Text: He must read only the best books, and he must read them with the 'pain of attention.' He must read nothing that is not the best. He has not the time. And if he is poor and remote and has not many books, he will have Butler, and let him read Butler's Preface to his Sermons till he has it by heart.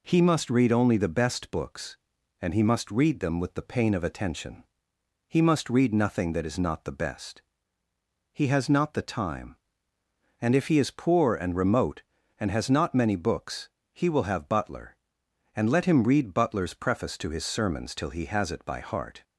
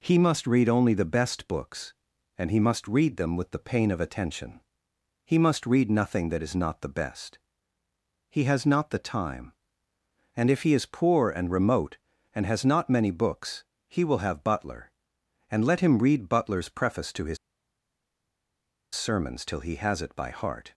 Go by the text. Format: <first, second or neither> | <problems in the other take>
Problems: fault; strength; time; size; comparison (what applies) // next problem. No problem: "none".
first | pauses between "his" and "Sermons"; strong; at 17.3 s; 1.5 s long